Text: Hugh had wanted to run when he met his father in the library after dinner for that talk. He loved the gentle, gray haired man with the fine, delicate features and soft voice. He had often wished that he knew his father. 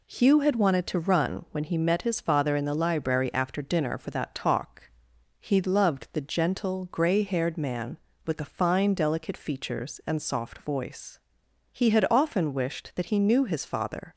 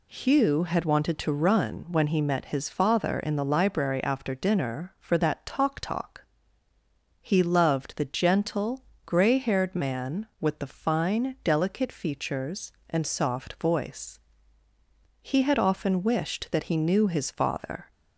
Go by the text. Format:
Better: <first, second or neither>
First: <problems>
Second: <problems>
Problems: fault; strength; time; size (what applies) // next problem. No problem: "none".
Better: first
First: none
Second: says "talk" twice; at 5.8 s